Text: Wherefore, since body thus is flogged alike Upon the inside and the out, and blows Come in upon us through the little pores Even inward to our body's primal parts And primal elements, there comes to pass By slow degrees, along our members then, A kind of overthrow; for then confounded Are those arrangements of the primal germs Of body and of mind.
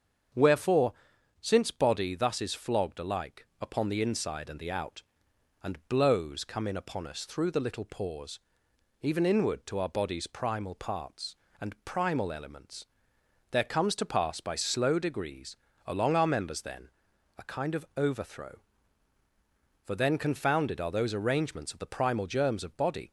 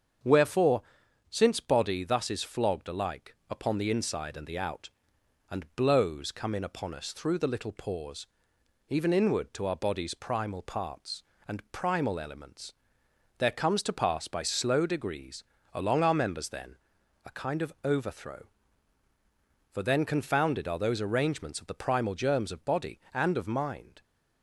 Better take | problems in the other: second | starts louder than the rest; until 1.8 s; 7 dB; also in the second // pauses between "pores" and "Even"; noticeable; at 8.3 s; 0.62 s long; noticeable in the second // stops before "and of mind"; at 23.0 s

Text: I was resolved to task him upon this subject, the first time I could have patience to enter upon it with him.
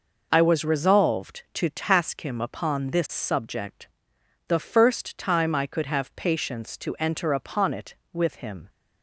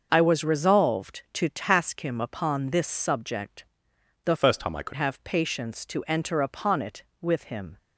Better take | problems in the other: first | starts louder than the rest; noticeable; until 1.1 s; 6 dB // changes voice from "first" to "could"; from 4.3 to 4.9 s; 0.6 s long

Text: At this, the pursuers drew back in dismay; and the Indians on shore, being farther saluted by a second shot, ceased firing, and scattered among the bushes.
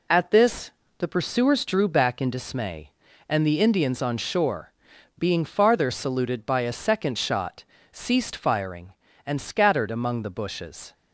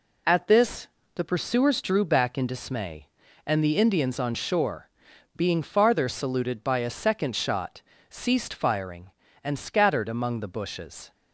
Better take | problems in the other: neither | none

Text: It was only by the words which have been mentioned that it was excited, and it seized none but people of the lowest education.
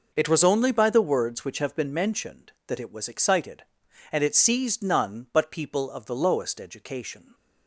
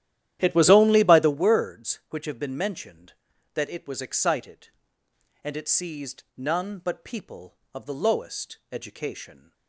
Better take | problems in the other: first | starts louder than the rest; strong; until 1.4 s; 12 dB // pauses between "lowest" and "education"; slight; at 8.5 s; 0.16 s long

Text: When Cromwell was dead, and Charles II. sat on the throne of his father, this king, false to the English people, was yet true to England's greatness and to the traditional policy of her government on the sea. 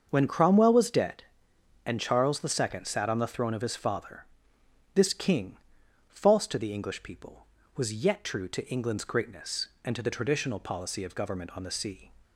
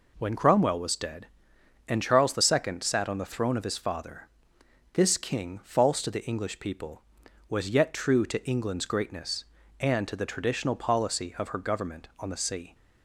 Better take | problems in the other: second | starts louder than the rest; until 1.1 s; 6.5 dB // skips "her"; at 11.1 s

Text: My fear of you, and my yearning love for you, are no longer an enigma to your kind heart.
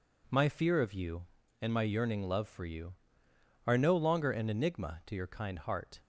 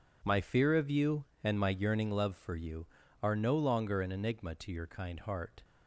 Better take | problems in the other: neither | none

